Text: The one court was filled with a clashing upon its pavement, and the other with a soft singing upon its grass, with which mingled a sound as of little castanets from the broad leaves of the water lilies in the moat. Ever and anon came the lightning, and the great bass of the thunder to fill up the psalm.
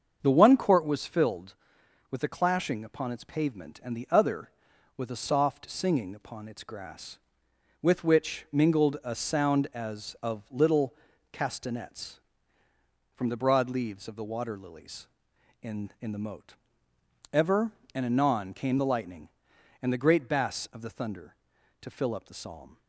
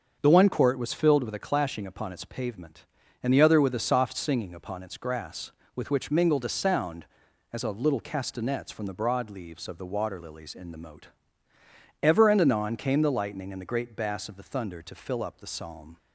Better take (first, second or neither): second